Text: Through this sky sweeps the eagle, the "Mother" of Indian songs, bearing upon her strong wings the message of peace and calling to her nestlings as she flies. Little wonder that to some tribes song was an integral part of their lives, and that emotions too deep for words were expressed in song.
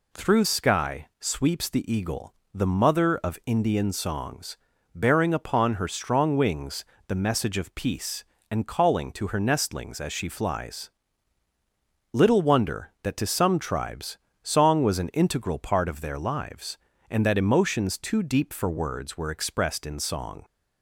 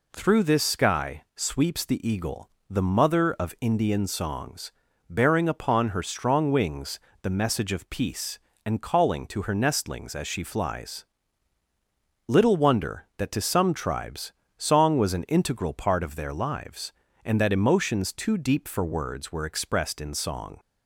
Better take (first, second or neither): second